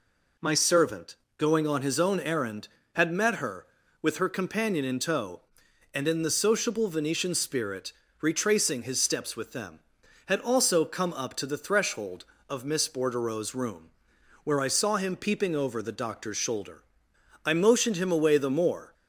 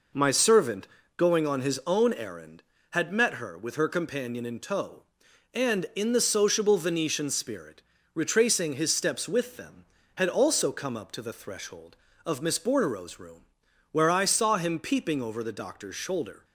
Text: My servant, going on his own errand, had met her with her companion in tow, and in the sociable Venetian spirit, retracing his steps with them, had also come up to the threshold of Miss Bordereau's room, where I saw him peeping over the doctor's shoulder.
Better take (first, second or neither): second